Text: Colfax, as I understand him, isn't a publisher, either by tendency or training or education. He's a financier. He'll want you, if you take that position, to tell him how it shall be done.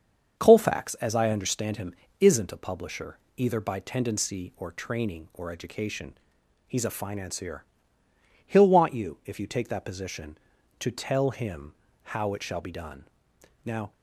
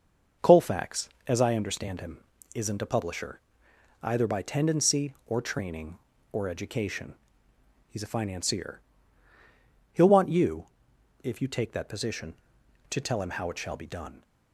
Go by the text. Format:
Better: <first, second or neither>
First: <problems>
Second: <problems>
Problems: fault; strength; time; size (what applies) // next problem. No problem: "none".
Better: second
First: starts louder than the rest; until 1.4 s; 7 dB // pauses between "him" and "how"; slight; at 11.7 s; 0.30 s long // goes on to say "Now"; slight; from 13.6 s on; 0.28 s long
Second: starts louder than the rest; noticeable; until 1.5 s; 6 dB